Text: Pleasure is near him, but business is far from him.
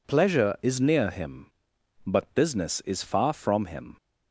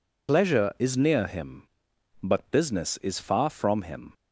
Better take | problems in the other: first | loses the start of "Pleasure"; at 0.2 s; 55 ms

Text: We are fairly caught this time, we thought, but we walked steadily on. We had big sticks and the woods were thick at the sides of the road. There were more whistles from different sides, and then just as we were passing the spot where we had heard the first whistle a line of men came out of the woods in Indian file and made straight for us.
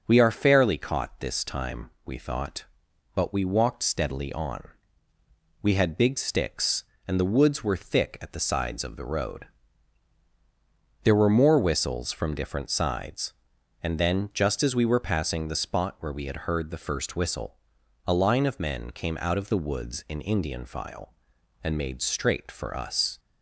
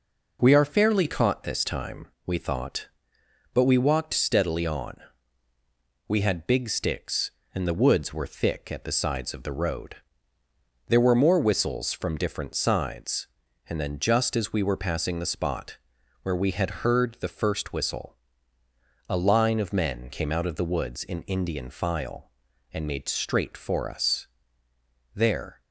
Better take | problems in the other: first | pauses between "spot" and "where"; noticeable; at 15.7 s; 0.46 s long // pauses between "whistle" and "a"; noticeable; at 18.1 s; 0.94 s long; noticeable in the first // goes on to say "There"; slight; from 25.1 s on; 0.46 s long

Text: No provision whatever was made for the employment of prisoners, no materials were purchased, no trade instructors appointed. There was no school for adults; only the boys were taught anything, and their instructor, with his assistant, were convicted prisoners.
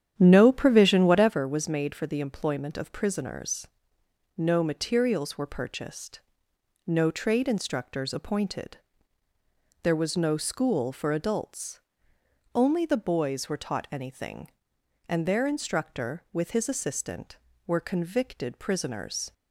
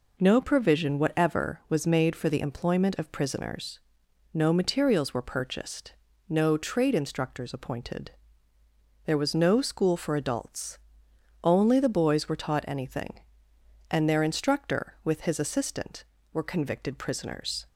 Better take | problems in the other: second | starts louder than the rest; strong; until 1.5 s; 9.5 dB

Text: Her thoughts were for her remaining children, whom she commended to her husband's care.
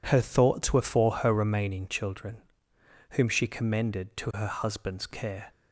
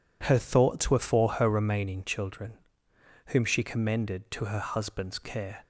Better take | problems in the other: neither | none

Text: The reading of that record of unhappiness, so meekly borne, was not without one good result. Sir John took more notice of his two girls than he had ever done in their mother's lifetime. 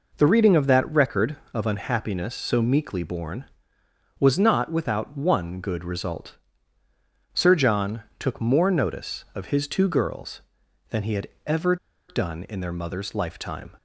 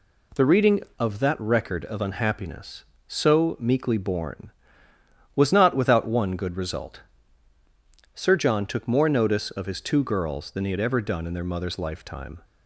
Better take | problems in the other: second | pauses between "John" and "took"; slight; at 8.0 s; 0.16 s long // pauses between "had" and "ever"; slight; at 11.2 s; 0.18 s long // pauses between "ever" and "done"; slight; at 11.7 s; 0.33 s long

